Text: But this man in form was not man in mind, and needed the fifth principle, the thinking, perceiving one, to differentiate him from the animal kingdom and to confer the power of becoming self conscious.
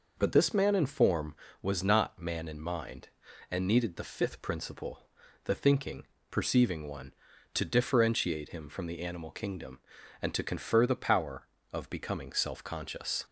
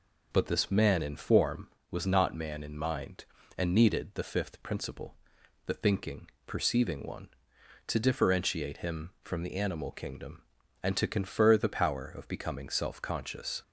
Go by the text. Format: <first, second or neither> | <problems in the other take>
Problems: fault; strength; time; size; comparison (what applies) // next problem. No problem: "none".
neither | none